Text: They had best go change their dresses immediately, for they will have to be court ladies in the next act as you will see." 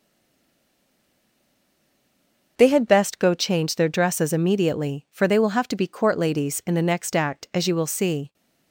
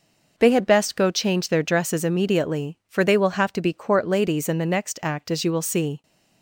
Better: second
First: stays silent before the first word; strong; until 2.5 s; 2.5 s long // starts louder than the rest; until 3.5 s; 6.5 dB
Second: none

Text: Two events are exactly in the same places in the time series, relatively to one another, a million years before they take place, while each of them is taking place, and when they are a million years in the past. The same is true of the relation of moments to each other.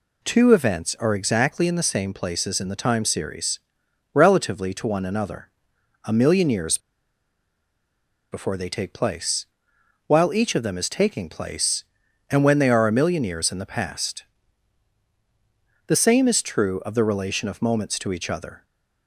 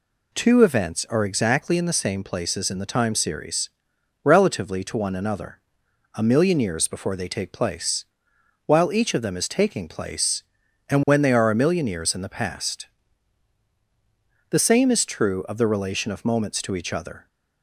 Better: second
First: pauses between "years" and "before"; strong; at 6.7 s; 1.5 s long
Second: none

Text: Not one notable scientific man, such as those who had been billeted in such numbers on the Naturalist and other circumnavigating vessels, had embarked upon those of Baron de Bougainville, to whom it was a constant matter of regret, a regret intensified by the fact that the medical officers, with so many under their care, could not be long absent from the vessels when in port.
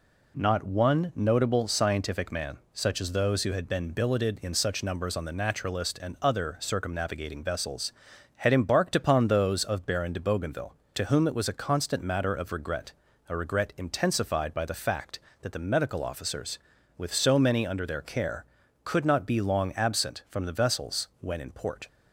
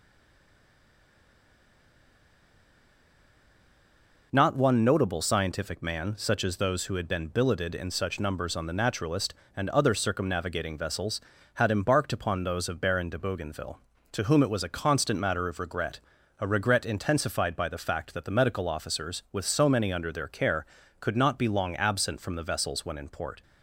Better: first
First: none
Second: stays silent before the first word; strong; until 4.3 s; 4.3 s long

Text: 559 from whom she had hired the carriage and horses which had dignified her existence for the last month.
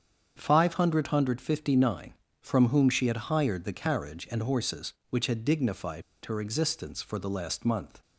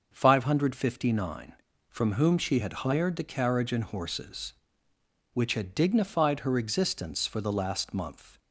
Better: second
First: starts louder than the rest; strong; until 1.3 s; 7.5 dB // pauses between "dignified" and "her"; slight; at 6.0 s; 0.23 s long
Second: starts louder than the rest; until 1.1 s; 6.5 dB

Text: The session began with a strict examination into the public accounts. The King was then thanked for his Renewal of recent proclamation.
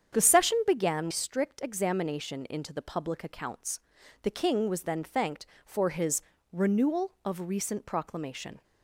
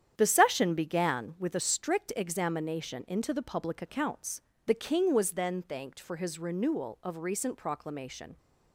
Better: second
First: starts louder than the rest; strong; until 1.1 s; 8 dB // skips "with a"; at 1.1 s // pauses between "his" and "Renewal"; slight; at 6.2 s; 0.32 s long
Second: starts louder than the rest; strong; until 1.1 s; 9.5 dB

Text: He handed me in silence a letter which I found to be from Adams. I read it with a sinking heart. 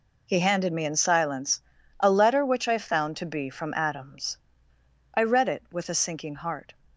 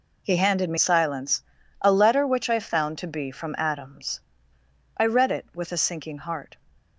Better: first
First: pauses between "silence" and "a"; at 1.6 s; 0.40 s long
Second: skips "in"; at 0.7 s // pauses between "silence" and "a"; at 1.4 s; 0.40 s long

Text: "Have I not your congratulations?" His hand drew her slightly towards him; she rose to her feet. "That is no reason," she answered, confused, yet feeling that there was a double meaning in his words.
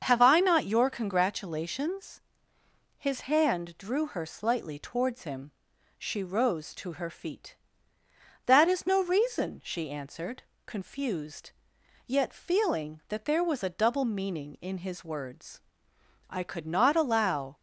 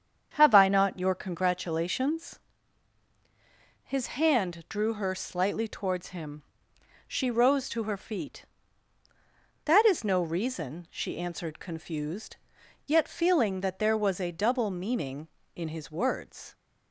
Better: second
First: starts louder than the rest; until 1.0 s; 7 dB // goes on to say "I could not allow"; noticeable; from 16.2 s on; 1.2 s long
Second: starts louder than the rest; strong; until 1.3 s; 7.5 dB

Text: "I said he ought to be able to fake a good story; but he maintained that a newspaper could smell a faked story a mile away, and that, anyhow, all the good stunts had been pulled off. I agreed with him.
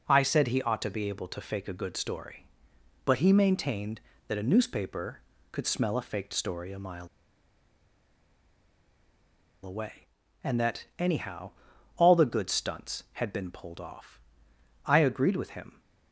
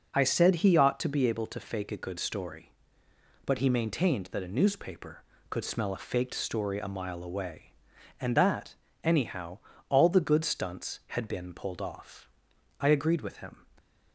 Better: second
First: pauses between "mile" and "away"; strong; at 7.0 s; 2.5 s long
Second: none

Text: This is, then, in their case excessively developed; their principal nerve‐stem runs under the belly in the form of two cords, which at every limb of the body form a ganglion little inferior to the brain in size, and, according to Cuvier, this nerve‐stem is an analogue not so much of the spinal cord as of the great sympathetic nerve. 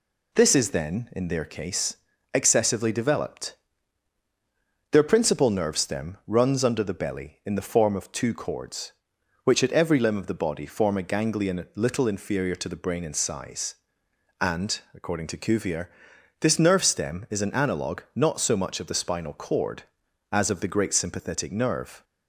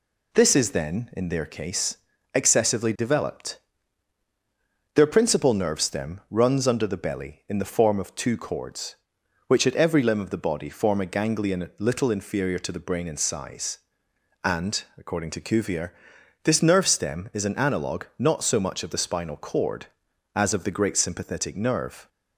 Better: neither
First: pauses between "case" and "excessively"; slight; at 1.9 s; 0.36 s long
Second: pauses between "case" and "excessively"; slight; at 1.9 s; 0.36 s long

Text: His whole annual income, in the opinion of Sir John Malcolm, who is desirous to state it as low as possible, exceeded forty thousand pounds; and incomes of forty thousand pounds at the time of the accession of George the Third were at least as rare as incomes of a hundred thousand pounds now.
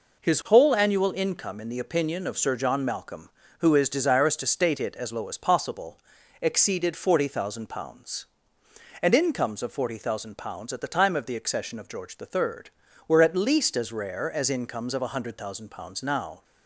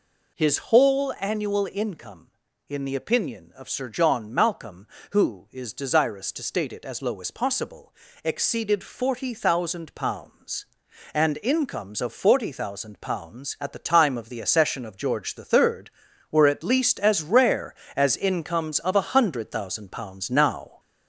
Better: first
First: none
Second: gets louder; slight; throughout; 3 dB

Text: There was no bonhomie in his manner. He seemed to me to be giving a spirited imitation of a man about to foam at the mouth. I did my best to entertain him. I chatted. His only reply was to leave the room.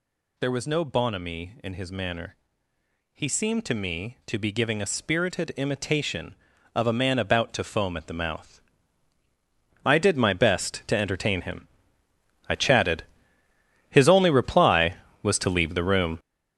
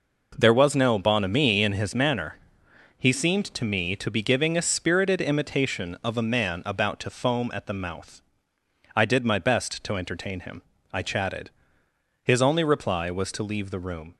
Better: second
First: gets louder; strong; throughout; 9.5 dB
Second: none

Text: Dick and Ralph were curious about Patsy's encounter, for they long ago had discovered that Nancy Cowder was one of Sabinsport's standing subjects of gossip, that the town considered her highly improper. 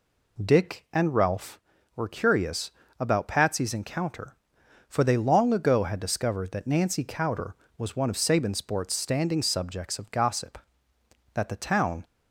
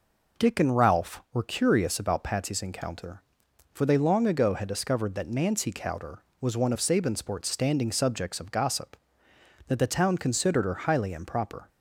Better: second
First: pauses between "curious" and "about"; slight; at 2.7 s; 0.28 s long // stops before "considered her highly improper"; at 12.0 s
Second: none

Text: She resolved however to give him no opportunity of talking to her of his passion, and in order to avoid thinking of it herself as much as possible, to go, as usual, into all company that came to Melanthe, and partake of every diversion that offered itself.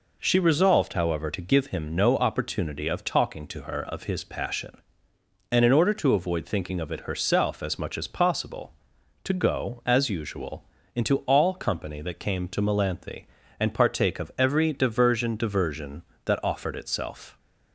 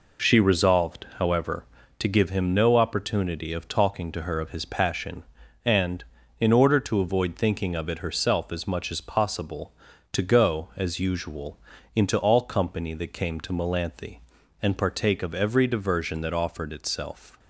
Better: second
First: says "diversion" twice; at 15.3 s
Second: none

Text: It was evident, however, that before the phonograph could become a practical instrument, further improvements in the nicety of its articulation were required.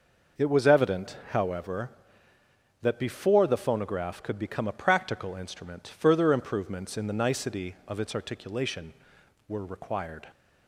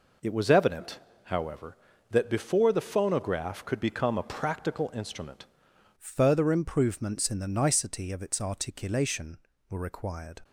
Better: first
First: none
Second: changes voice at "further"; from 5.9 s on; 4.5 s long

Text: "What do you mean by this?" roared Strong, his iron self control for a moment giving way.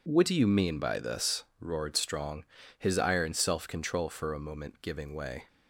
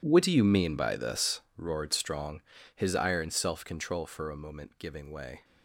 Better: first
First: none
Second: gets quieter; strong; throughout; 18 dB

